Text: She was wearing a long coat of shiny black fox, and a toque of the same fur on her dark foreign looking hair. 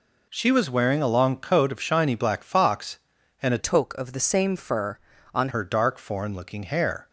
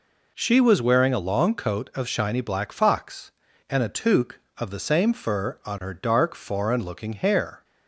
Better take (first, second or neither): second